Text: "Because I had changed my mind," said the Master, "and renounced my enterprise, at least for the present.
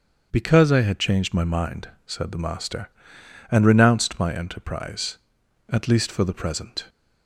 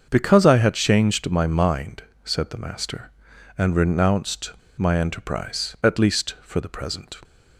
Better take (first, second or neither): first